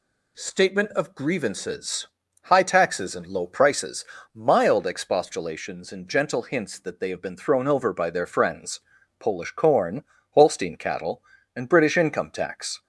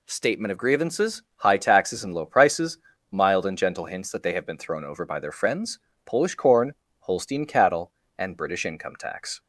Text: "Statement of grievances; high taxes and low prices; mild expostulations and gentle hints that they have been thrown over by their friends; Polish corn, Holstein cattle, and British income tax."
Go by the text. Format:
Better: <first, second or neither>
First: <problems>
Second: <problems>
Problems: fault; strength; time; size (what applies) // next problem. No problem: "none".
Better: first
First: none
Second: skips "expostulations"; at 3.4 s